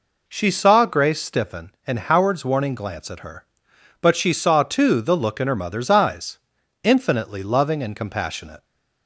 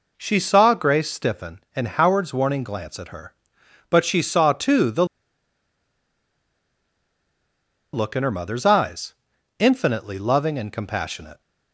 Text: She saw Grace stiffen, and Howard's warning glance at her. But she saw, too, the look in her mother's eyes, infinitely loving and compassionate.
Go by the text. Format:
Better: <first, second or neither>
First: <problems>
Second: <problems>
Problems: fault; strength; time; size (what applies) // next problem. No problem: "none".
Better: first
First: none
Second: pauses between "the" and "look"; strong; at 5.0 s; 2.8 s long